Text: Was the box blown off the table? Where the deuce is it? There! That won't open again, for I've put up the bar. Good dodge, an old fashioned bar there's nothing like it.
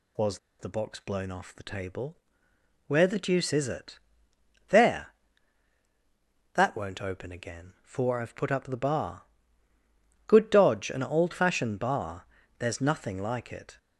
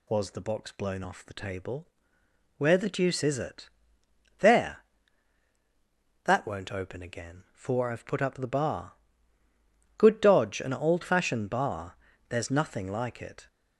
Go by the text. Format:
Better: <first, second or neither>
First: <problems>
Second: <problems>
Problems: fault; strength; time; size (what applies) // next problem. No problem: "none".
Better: second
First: pauses between "Was" and "the"; slight; at 0.3 s; 0.22 s long // pauses between "bar" and "there's"; slight; at 12.2 s; 0.32 s long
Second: pauses between "bar" and "there's"; slight; at 11.9 s; 0.32 s long